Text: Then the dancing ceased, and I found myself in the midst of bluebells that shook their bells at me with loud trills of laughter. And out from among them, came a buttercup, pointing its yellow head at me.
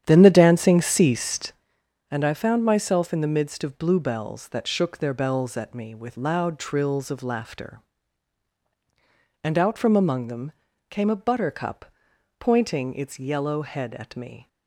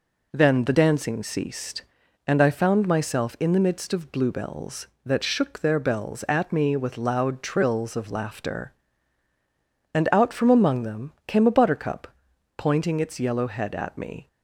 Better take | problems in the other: second | starts louder than the rest; strong; until 1.7 s; 9.5 dB

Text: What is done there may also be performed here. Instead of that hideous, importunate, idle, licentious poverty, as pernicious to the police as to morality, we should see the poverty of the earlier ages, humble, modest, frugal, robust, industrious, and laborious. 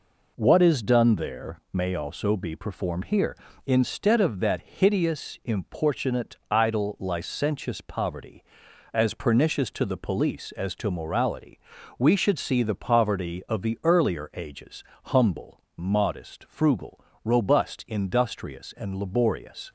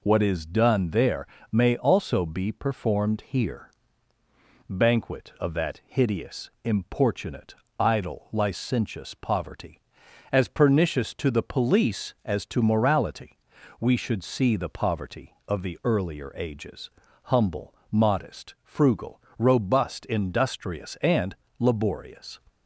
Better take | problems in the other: first | pauses between "there" and "may"; slight; at 1.2 s; 0.24 s long // says "Banquet" for "Instead"; at 4.6 s // pauses between "and" and "laborious"; slight; at 21.3 s; 0.24 s long

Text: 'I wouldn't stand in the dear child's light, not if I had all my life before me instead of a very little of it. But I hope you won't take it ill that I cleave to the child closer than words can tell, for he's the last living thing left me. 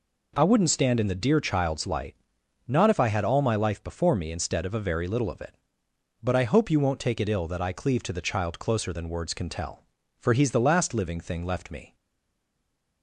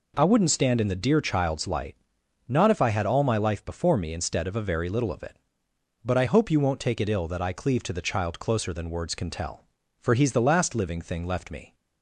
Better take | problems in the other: second | stays silent after the last word; from 11.9 s on; 1.1 s long

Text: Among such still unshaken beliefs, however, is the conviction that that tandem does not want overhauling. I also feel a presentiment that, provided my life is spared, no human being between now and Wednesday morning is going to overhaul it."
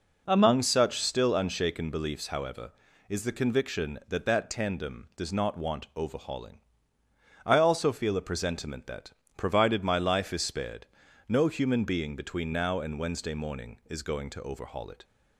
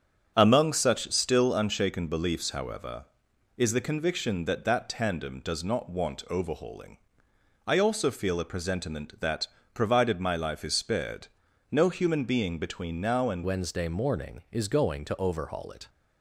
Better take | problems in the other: first | starts louder than the rest; strong; until 1.3 s; 7.5 dB // changes voice at "Wednesday"; from 13.4 s on; 2.4 s long

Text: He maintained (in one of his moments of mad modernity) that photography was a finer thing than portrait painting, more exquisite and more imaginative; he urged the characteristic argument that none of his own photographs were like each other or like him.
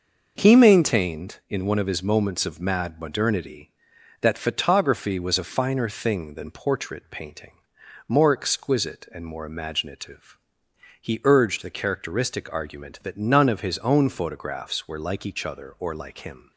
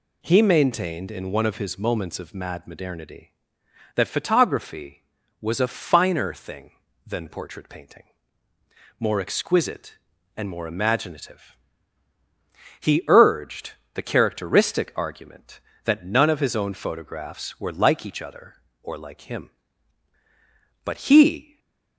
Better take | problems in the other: first | pauses between "urged" and "the"; slight; at 13.7 s; 0.22 s long // goes on to say "But he"; noticeable; from 20.8 s on; 0.74 s long // stays silent after the last word; slight; from 21.4 s on; 0.5 s long

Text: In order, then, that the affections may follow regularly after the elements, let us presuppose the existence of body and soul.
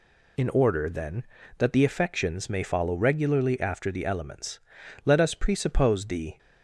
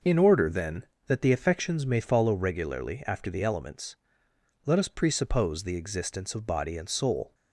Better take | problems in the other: second | stops before "existence of body and soul"; at 6.3 s

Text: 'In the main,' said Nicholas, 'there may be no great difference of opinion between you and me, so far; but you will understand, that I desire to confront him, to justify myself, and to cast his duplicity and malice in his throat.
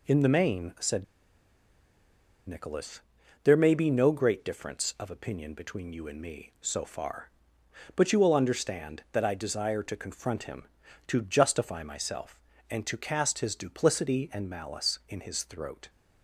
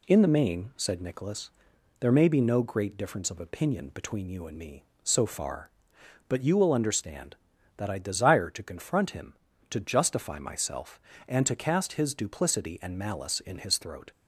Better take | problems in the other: second | pauses between "said" and "Nicholas"; strong; at 1.0 s; 1.4 s long

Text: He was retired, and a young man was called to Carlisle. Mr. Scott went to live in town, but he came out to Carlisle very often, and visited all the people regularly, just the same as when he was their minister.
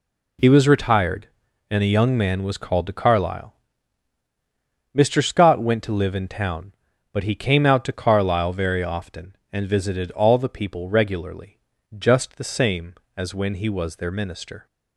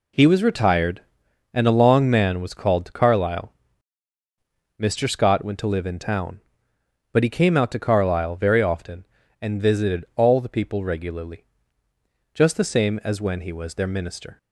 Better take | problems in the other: first | says "long" for "young"; at 1.8 s

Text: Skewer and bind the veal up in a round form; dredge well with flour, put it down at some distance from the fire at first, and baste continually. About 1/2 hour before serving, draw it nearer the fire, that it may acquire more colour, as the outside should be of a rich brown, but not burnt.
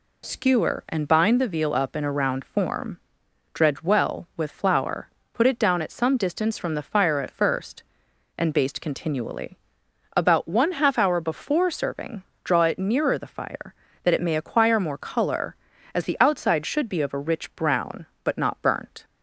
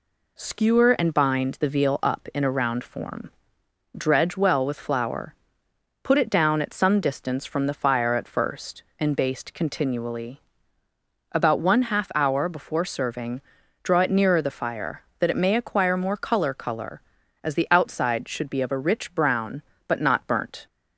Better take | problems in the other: first | says "colour" twice; at 16.5 s

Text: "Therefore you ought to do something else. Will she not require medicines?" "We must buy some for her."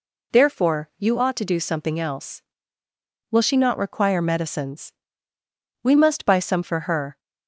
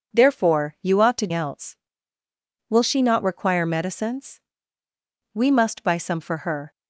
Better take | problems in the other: first | skips "do something"; at 1.3 s

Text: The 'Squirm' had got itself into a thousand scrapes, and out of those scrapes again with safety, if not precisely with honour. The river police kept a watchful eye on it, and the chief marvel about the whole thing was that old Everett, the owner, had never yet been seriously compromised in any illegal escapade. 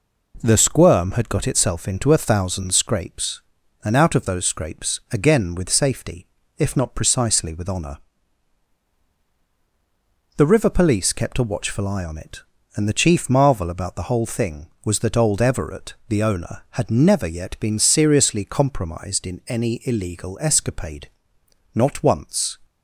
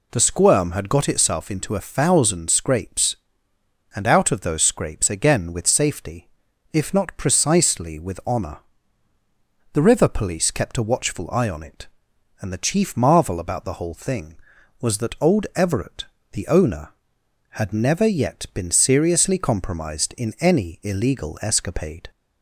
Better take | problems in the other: second | goes on to say "Not once"; noticeable; from 21.7 s on; 0.84 s long

